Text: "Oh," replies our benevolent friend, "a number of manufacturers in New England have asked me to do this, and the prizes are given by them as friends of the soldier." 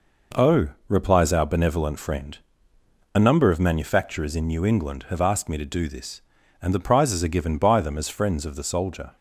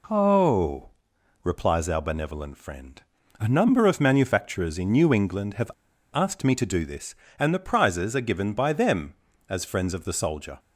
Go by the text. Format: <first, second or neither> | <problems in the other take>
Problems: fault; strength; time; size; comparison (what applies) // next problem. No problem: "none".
first | pauses between "have" and "asked"; at 5.7 s; 0.41 s long